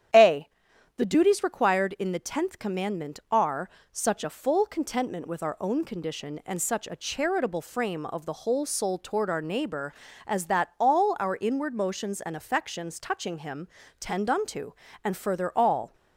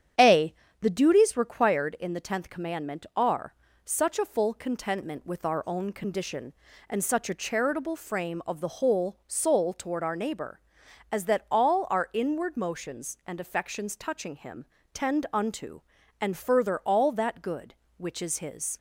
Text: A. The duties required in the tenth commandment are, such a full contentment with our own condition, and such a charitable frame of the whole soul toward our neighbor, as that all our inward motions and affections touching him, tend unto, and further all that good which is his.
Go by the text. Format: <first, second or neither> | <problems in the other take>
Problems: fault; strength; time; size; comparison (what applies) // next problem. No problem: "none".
second | starts louder than the rest; strong; until 1.6 s; 9.5 dB; strong in the second // stops before "that good which is his"; at 15.9 s